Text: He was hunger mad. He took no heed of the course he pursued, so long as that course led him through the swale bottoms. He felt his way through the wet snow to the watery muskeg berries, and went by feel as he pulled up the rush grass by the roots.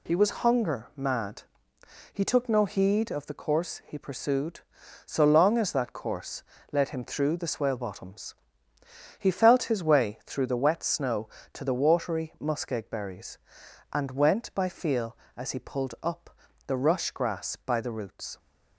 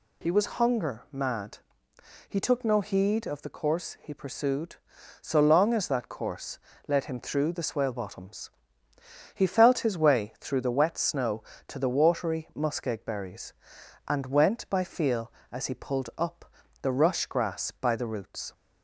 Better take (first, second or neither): second